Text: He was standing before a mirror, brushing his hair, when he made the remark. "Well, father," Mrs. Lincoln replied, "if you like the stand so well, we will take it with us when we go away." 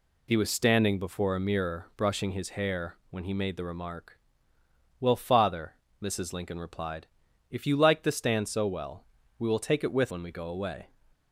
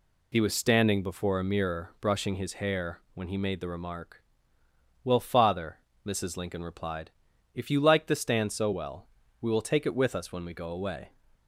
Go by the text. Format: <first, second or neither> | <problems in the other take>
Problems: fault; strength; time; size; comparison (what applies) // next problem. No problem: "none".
second | skips "us"; at 10.1 s